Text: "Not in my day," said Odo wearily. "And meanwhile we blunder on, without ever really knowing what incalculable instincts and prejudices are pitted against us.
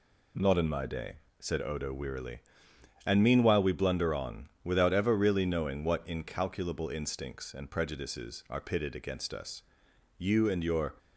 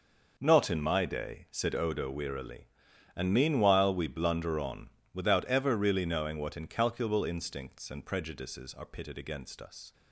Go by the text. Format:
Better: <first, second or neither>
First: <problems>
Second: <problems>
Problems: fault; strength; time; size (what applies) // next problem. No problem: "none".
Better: second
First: goes on to say "You and your"; noticeable; from 10.1 s on; 0.76 s long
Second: none